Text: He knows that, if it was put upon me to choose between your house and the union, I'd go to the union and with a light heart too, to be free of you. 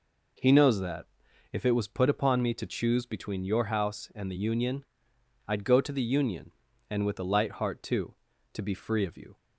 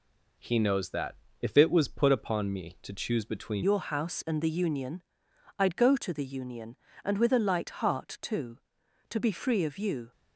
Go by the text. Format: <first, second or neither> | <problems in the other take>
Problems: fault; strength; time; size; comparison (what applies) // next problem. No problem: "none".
first | changes voice at "your"; from 3.6 s on; 6.5 s long